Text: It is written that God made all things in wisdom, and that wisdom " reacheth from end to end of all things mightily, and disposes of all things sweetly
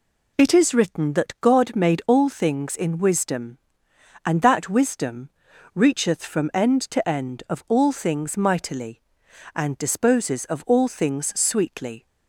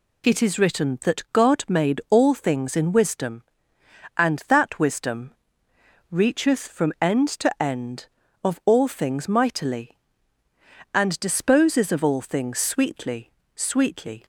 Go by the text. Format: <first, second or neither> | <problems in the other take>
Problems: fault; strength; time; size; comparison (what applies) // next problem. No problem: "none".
first | says "sweetly" twice; at 13.5 s